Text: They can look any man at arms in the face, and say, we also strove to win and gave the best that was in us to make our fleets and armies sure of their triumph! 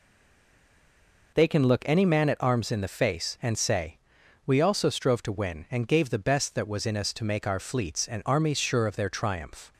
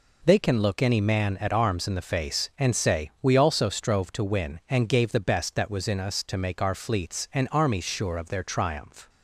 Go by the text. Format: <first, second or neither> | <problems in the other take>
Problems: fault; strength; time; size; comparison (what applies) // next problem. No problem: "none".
second | stays silent before the first word; noticeable; until 1.3 s; 1.3 s long